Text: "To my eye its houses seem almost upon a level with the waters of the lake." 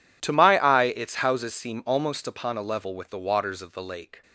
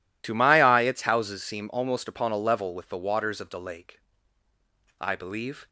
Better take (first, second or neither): first